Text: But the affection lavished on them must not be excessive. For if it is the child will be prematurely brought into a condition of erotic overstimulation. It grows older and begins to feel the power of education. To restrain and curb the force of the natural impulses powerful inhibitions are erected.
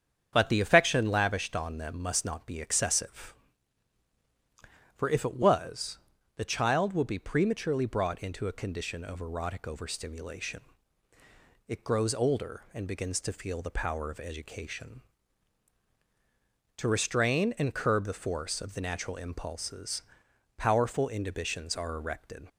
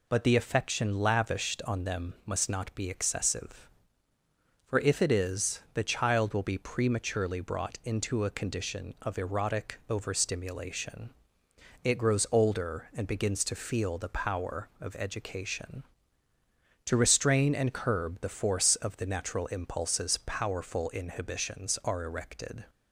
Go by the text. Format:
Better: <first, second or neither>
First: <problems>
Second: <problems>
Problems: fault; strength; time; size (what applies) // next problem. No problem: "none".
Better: second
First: starts louder than the rest; strong; until 1.3 s; 8 dB // says "was" for "is"; at 5.3 s // pauses between "impulses" and "powerful"; noticeable; at 20.0 s; 0.54 s long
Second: none